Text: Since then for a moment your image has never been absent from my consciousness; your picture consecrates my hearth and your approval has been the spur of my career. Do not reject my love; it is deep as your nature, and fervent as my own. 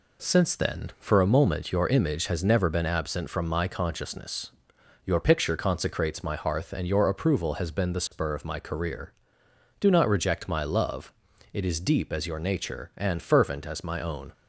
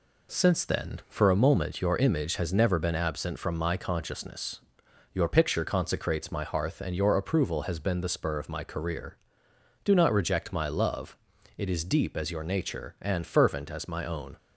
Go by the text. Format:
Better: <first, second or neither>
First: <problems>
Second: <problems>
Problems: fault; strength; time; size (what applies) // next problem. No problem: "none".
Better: neither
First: none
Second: none